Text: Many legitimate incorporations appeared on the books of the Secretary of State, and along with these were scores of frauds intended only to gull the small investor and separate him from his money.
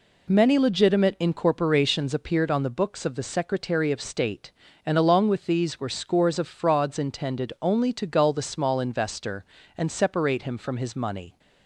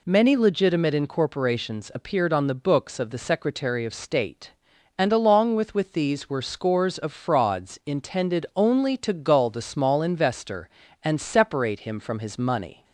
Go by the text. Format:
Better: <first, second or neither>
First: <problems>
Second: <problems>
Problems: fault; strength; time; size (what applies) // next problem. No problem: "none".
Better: first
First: none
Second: says "with" twice; at 5.7 s